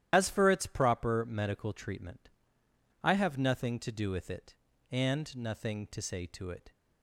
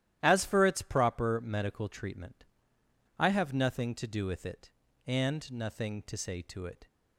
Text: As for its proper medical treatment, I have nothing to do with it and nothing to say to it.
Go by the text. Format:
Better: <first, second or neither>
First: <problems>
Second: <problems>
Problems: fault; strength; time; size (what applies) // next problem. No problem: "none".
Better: second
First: loses the start of "As"; at 0.1 s; 60 ms // starts louder than the rest; strong; until 1.1 s; 12 dB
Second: starts louder than the rest; strong; until 1.2 s; 12.5 dB